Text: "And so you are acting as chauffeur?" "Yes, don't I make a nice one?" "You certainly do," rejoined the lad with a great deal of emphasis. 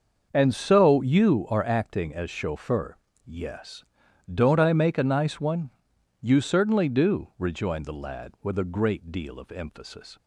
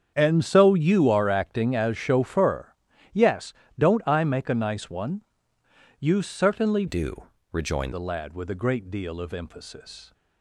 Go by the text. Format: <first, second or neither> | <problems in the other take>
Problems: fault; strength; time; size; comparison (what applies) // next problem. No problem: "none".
first | starts louder than the rest; strong; until 1.1 s; 7.5 dB; also in the first // changes voice from "do" to "rejoined"; from 6.8 to 7.9 s; 1.1 s long